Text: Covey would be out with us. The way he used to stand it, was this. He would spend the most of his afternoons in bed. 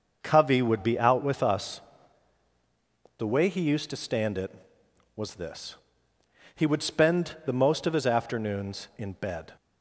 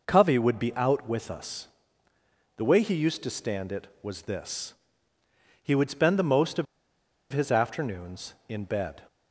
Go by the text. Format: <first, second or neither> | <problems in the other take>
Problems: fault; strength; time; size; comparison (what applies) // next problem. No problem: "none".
first | pauses between "of" and "his"; noticeable; at 6.6 s; 0.67 s long